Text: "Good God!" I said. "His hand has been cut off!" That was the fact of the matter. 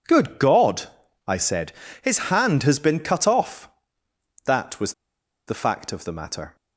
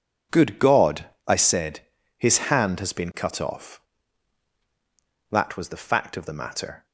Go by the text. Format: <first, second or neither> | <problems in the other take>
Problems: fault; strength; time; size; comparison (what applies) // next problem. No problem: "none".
second | pauses between "was" and "the"; noticeable; at 4.9 s; 0.55 s long